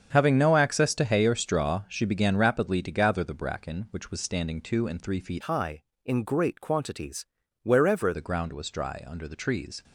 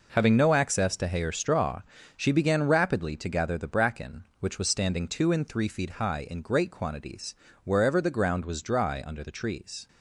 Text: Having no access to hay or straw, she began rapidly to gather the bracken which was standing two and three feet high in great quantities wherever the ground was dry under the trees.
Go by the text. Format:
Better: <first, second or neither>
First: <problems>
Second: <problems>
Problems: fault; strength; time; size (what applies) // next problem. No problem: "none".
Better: second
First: starts louder than the rest; strong; until 1.1 s; 7.5 dB // changes voice from "high" to "wherever"; from 5.4 to 8.1 s; 2.7 s long // pauses between "quantities" and "wherever"; slight; at 7.2 s; 0.36 s long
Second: pauses between "quantities" and "wherever"; slight; at 7.3 s; 0.28 s long